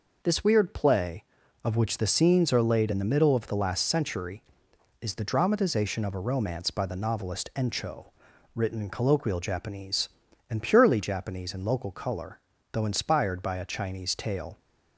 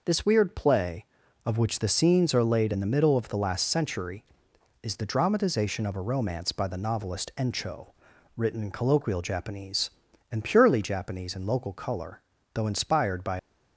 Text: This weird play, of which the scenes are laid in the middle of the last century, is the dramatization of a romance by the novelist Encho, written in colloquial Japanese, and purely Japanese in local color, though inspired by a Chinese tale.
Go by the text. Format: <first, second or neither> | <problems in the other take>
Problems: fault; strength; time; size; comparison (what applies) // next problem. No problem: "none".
first | stops before "a Chinese tale"; at 13.3 s